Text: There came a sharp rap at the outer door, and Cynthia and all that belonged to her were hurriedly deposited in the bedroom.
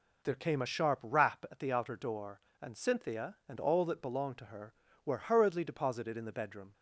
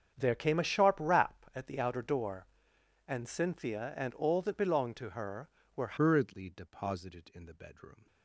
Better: first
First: none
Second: starts louder than the rest; strong; until 1.1 s; 7.5 dB // changes voice at "hurriedly"; from 5.9 s on; 2.1 s long

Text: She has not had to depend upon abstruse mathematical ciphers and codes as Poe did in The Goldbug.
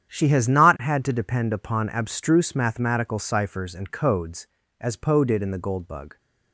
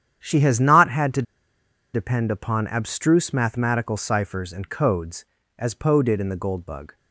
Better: first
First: starts louder than the rest; strong; until 1.1 s; 9 dB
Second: starts louder than the rest; strong; until 1.2 s; 9 dB // pauses between "to" and "depend"; noticeable; at 1.2 s; 0.71 s long

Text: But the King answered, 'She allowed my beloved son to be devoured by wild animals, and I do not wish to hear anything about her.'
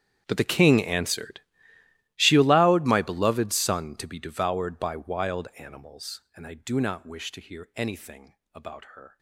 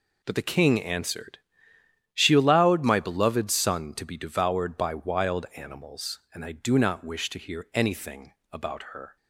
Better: second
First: gets quieter; strong; throughout; 21.5 dB // pauses between "anything" and "about"; slight; at 8.3 s; 0.18 s long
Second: pauses between "anything" and "about"; slight; at 8.3 s; 0.18 s long

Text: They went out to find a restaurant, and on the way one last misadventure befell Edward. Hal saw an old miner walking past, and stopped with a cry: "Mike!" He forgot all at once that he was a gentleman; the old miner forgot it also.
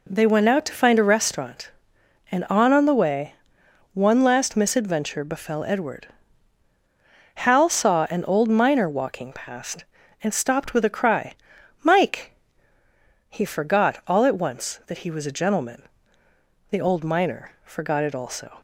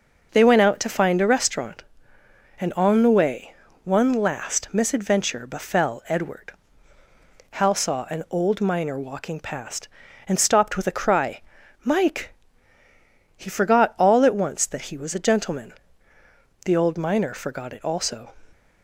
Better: second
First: says "on" twice; at 2.7 s // pauses between "way" and "one"; noticeable; at 3.3 s; 0.60 s long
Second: pauses between "way" and "one"; slight; at 3.5 s; 0.30 s long

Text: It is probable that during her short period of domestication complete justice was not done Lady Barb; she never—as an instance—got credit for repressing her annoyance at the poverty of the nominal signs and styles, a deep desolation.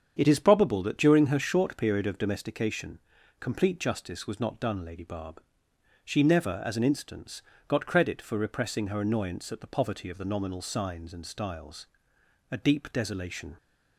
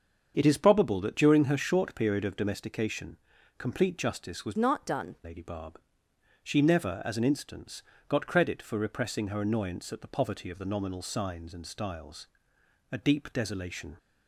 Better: first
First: starts louder than the rest; strong; until 1.1 s; 7.5 dB // pauses between "domestication" and "complete"; at 2.9 s; 0.42 s long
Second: starts louder than the rest; until 1.3 s; 7 dB // pauses between "domestication" and "complete"; at 3.1 s; 0.42 s long // changes voice from "not" to "done"; from 4.5 to 5.1 s; 0.6 s long

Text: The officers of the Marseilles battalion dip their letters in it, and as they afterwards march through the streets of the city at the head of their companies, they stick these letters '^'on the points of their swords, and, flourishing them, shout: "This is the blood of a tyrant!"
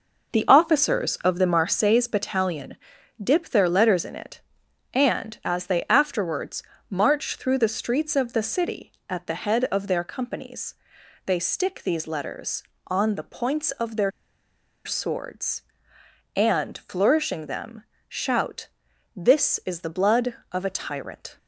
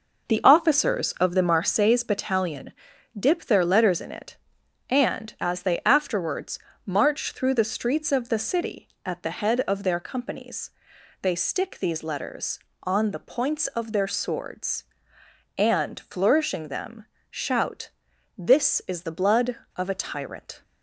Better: second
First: pauses between "battalion" and "dip"; noticeable; at 2.7 s; 0.46 s long // pauses between "afterwards" and "march"; slight; at 6.6 s; 0.28 s long // pauses between "their" and "swords"; noticeable; at 14.0 s; 0.75 s long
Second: pauses between "battalion" and "dip"; noticeable; at 2.7 s; 0.46 s long // pauses between "afterwards" and "march"; slight; at 6.5 s; 0.28 s long

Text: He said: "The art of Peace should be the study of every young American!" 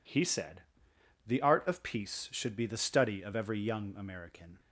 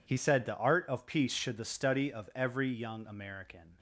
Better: first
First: none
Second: skips "be"; at 1.5 s

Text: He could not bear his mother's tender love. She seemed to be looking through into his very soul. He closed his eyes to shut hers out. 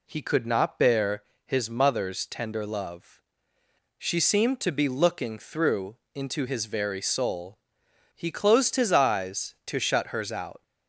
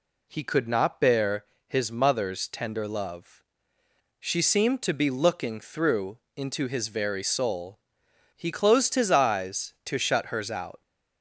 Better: neither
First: pauses between "bear" and "his"; slight; at 1.2 s; 0.22 s long // pauses between "through" and "into"; slight; at 5.9 s; 0.18 s long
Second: pauses between "bear" and "his"; slight; at 1.4 s; 0.22 s long // pauses between "through" and "into"; slight; at 6.1 s; 0.18 s long

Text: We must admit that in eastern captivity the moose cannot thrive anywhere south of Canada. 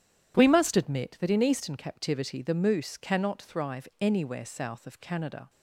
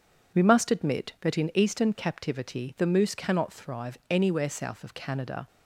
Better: neither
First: none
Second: none

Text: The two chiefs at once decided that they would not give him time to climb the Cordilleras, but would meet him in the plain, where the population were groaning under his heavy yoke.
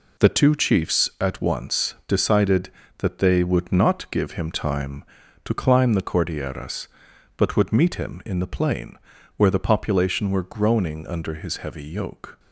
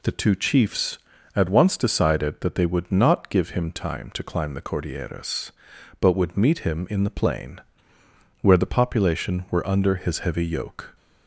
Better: first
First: none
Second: skips "groaning"; at 9.6 s

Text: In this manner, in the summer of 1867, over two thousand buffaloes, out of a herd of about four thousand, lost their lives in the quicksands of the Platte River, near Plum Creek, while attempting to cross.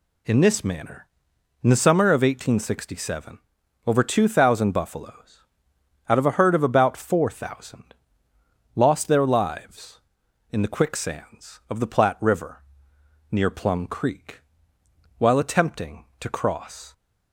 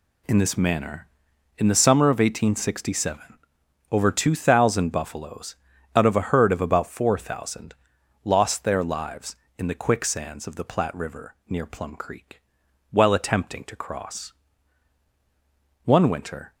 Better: first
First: none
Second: goes on to say "One winter"; noticeable; from 15.8 s on; 0.70 s long

